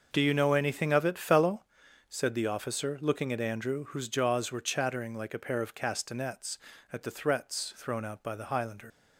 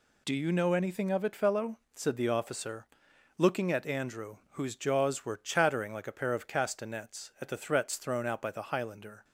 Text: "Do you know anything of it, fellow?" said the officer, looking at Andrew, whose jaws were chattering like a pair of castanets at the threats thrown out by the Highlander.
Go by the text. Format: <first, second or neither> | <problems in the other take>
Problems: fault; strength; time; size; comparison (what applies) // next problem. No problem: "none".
second | starts louder than the rest; until 1.1 s; 6 dB // leaves "Highlander" unfinished; at 8.9 s; 95 ms